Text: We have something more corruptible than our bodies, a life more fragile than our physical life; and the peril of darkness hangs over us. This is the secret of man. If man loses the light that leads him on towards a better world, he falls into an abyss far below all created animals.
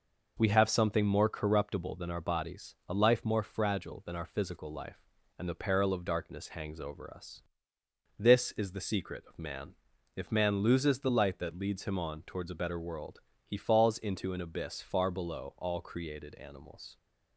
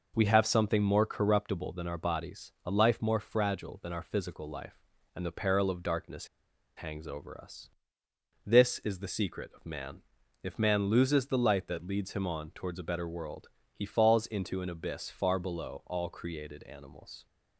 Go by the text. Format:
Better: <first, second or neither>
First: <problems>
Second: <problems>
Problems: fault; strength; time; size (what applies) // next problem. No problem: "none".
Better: first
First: none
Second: pauses between "darkness" and "hangs"; noticeable; at 6.2 s; 0.49 s long